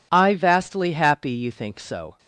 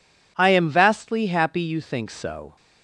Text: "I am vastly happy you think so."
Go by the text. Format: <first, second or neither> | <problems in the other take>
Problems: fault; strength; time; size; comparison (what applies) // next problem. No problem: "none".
second | skips "am"; at 0.3 s